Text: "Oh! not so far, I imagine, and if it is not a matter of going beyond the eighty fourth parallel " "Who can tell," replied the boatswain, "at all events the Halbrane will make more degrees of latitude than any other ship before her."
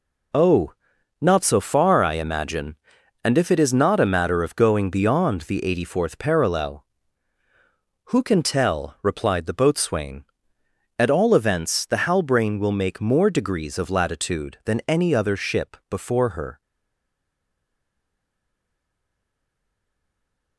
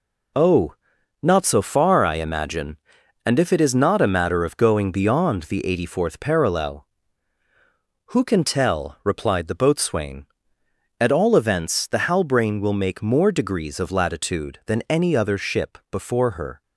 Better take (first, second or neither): second